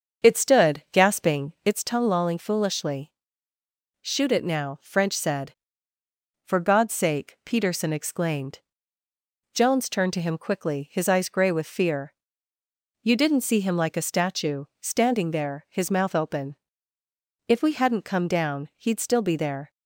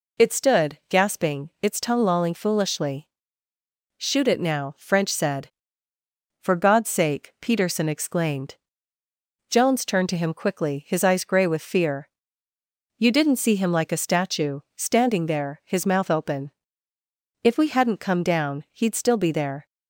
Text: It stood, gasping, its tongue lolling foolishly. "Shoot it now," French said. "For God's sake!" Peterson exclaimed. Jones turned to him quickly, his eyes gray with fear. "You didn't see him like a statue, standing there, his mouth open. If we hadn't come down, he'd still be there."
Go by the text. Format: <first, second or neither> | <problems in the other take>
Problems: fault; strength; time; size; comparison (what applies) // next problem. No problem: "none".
second | starts louder than the rest; until 1.9 s; 7 dB